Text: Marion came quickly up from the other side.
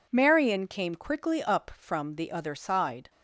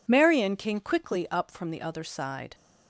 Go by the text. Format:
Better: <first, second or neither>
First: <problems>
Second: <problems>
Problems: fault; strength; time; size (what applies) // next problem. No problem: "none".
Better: neither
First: none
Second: none